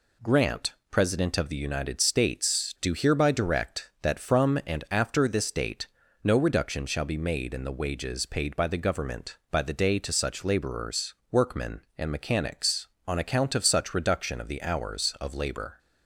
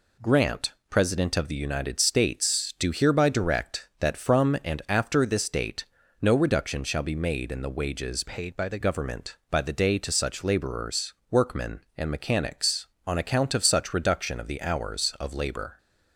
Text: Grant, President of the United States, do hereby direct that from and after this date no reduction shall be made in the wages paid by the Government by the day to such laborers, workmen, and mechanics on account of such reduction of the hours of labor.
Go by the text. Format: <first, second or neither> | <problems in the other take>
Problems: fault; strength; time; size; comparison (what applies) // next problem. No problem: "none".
first | pauses between "date" and "no"; at 5.8 s; 0.38 s long; also in the first // changes voice from "paid" to "the"; from 8.2 to 8.7 s; 0.5 s long